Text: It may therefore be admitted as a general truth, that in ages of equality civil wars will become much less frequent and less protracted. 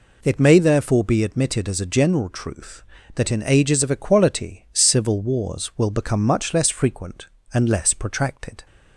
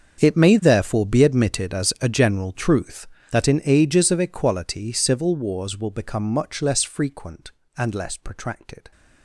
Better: first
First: none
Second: gets quieter; strong; throughout; 18 dB

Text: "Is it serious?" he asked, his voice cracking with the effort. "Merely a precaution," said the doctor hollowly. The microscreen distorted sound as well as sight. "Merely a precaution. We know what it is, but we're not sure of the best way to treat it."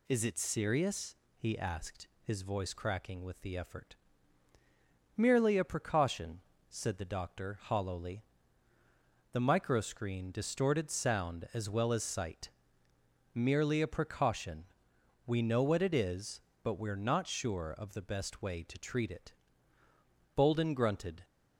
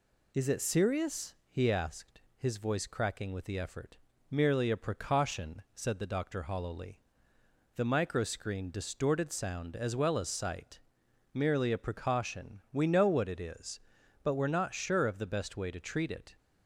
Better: second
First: goes on to say "Bolden grunted"; noticeable; from 20.3 s on; 0.88 s long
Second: none

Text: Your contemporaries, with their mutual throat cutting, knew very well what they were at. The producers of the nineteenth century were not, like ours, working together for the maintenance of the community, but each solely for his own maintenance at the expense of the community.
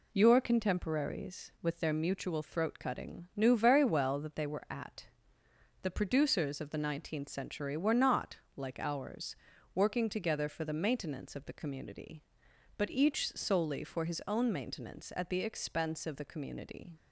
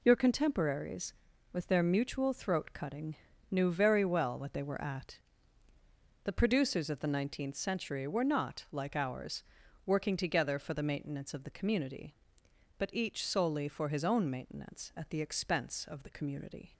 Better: second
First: says "that" for "what"; at 4.1 s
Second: none

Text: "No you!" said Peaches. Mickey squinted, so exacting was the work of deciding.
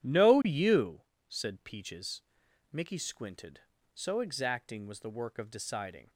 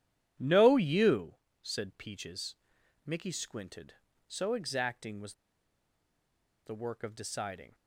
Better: first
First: none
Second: pauses between "was" and "the"; strong; at 5.3 s; 1.3 s long

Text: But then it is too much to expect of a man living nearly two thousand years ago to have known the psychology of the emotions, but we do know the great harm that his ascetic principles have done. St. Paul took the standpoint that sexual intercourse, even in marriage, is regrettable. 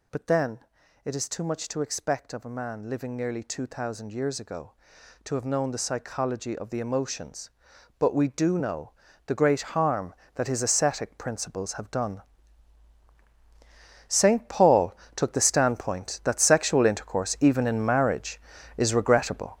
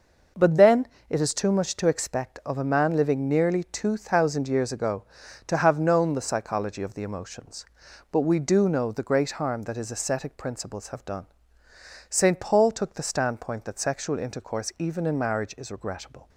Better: second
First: gets louder; strong; throughout; 9.5 dB // pauses between "then" and "it"; at 0.5 s; 0.44 s long // pauses between "know" and "the"; slight; at 8.9 s; 0.36 s long // pauses between "great" and "harm"; slight; at 9.6 s; 0.16 s long // pauses between "Paul" and "took"; slight; at 14.9 s; 0.20 s long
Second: pauses between "then" and "it"; slight; at 0.8 s; 0.22 s long

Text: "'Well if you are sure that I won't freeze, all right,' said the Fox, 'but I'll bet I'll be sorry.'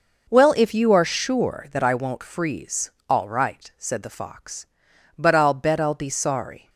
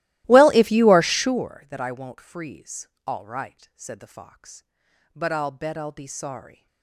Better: first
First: none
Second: starts louder than the rest; strong; until 1.5 s; 16.5 dB

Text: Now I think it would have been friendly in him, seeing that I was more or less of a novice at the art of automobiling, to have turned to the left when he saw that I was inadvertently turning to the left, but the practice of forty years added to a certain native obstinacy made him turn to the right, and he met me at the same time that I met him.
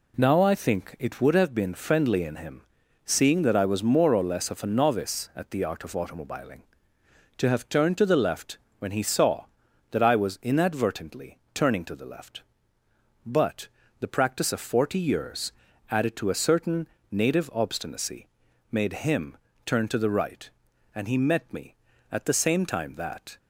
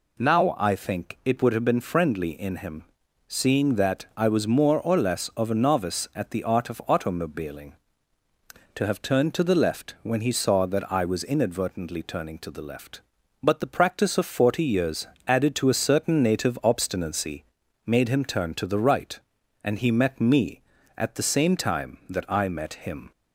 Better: second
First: pauses between "left" and "when"; slight; at 8.5 s; 0.22 s long // pauses between "inadvertently" and "turning"; slight; at 11.3 s; 0.16 s long // pauses between "but" and "the"; slight; at 13.6 s; 0.32 s long // pauses between "years" and "added"; at 15.5 s; 0.40 s long // pauses between "certain" and "native"; slight; at 16.8 s; 0.24 s long // pauses between "obstinacy" and "made"; at 18.2 s; 0.44 s long // pauses between "him" and "turn"; slight; at 19.3 s; 0.30 s long // stops before "I met him"; at 23.3 s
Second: pauses between "years" and "added"; slight; at 15.0 s; 0.22 s long // pauses between "obstinacy" and "made"; at 17.4 s; 0.42 s long

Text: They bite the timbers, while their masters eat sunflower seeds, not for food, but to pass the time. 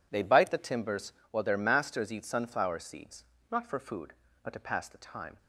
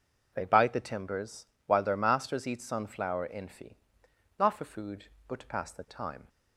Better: first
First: none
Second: says "infi" for "seeds"; at 3.2 s

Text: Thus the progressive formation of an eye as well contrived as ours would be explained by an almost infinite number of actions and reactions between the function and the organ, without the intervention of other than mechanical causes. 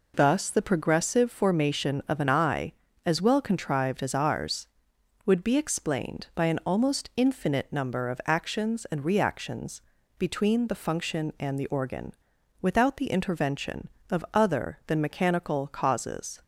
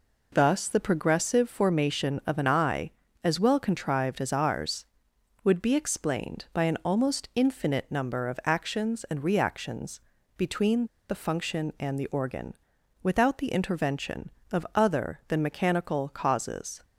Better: first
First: pauses between "reactions" and "between"; at 9.8 s; 0.38 s long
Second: pauses between "reactions" and "between"; at 9.9 s; 0.38 s long // pauses between "between" and "the"; slight; at 10.8 s; 0.22 s long

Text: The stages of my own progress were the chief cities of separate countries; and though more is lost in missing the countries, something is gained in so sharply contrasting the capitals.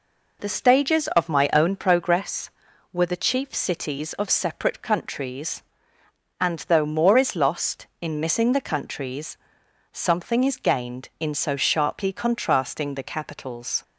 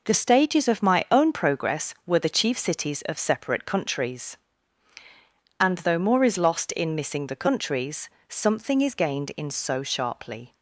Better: first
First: none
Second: stops before "contrasting the capitals"; at 10.5 s

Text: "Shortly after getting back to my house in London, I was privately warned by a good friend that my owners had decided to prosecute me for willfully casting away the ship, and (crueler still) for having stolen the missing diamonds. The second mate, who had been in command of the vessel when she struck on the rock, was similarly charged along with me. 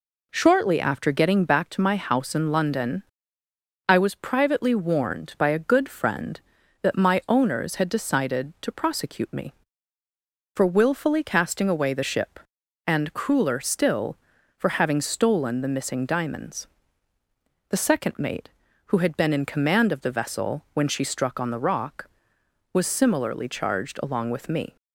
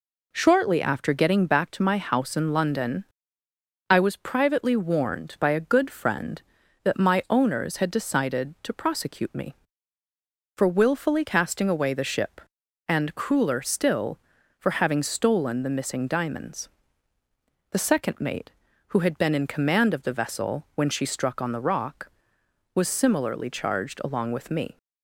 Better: neither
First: none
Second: none

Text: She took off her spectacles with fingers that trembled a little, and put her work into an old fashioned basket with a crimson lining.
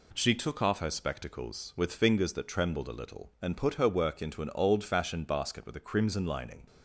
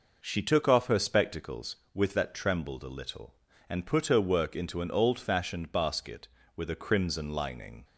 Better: first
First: none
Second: skips "fingers"; at 2.1 s

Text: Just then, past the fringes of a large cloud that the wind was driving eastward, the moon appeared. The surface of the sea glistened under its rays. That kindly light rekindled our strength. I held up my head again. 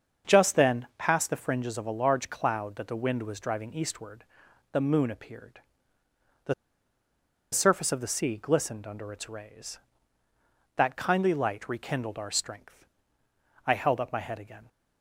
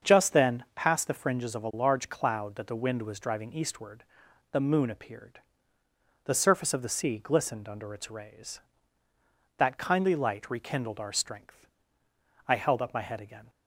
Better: second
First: starts louder than the rest; until 1.3 s; 7 dB // pauses between "The" and "surface"; at 6.5 s; 1.0 s long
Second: starts louder than the rest; until 1.1 s; 7 dB

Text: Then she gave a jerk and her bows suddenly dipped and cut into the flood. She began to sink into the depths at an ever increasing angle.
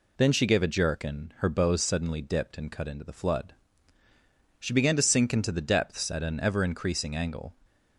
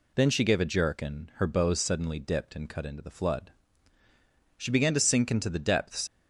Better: first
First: none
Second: stops before "at an ever increasing angle"; at 6.0 s

